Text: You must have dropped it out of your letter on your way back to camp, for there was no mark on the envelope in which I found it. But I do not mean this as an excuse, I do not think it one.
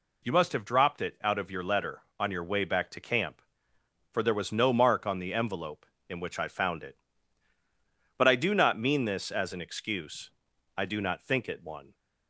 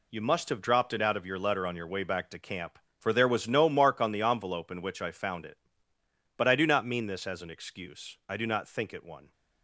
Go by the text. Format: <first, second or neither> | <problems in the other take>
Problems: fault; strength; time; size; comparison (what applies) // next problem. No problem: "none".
first | gets quieter; strong; throughout; 9 dB